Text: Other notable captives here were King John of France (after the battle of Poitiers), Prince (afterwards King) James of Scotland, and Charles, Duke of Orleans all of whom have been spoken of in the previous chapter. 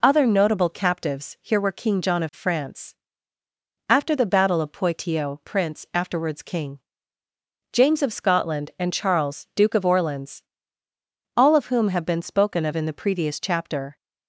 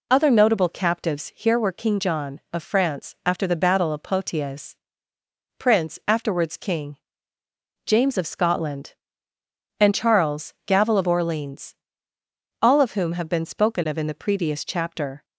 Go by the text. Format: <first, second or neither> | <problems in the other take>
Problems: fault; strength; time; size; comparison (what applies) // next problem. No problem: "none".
first | says "Gavel" for "Duke"; at 10.6 s // pauses between "Orleans" and "all"; noticeable; at 11.7 s; 0.88 s long; noticeable in the first